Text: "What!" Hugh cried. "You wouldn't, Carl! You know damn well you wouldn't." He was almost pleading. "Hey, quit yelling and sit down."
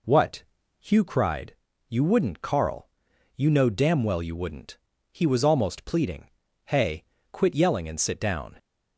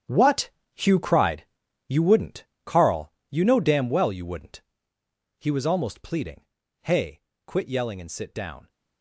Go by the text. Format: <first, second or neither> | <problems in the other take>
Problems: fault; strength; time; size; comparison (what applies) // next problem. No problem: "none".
first | gets quieter; strong; throughout; 13.5 dB